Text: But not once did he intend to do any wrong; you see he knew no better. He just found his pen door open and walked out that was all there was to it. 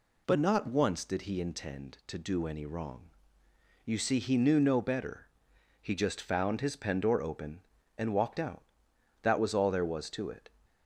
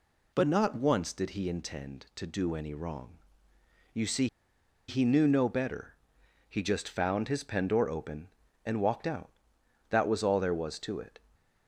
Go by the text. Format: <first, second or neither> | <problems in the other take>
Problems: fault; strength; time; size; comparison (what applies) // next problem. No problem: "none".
first | pauses between "see" and "he"; noticeable; at 4.2 s; 0.61 s long